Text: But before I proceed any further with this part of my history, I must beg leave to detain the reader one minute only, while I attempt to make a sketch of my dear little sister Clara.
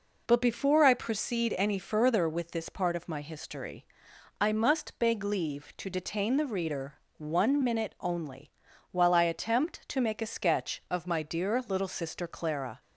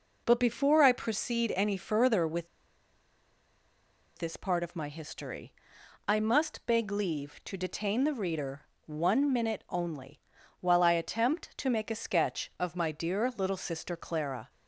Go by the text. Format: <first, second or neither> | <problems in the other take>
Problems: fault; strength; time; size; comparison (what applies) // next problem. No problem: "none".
first | pauses between "with" and "this"; strong; at 2.4 s; 1.6 s long // pauses between "reader" and "one"; slight; at 8.6 s; 0.24 s long; slight in the first